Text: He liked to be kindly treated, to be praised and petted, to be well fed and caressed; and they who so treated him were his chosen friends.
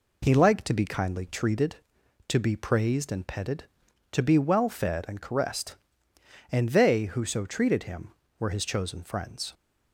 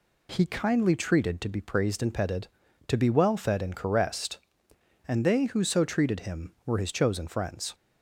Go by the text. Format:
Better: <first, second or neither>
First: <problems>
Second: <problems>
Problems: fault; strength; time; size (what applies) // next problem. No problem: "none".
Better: first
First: none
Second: skips "liked to be"; at 0.4 s